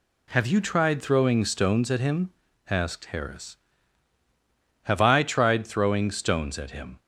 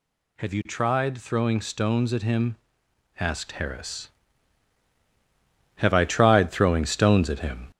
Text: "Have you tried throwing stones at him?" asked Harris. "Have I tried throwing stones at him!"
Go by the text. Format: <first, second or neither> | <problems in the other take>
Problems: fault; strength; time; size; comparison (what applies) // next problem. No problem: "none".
first | gets louder; slight; throughout; 3 dB